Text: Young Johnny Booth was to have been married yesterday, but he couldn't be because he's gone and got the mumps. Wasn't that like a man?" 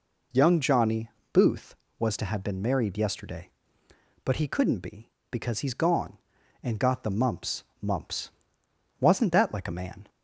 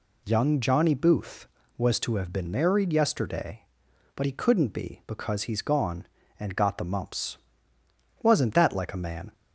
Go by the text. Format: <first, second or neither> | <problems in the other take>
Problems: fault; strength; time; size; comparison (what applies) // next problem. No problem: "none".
second | pauses between "Johnny" and "Booth"; slight; at 1.1 s; 0.22 s long // says "mumps" twice; at 7.8 s